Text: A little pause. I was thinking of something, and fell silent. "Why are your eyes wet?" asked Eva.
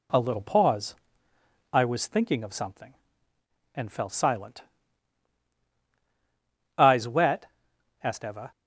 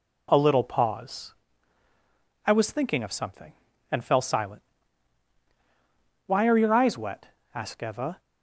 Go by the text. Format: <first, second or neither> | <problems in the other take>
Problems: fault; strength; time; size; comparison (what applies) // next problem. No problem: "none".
second | skips "Why are your"; at 5.6 s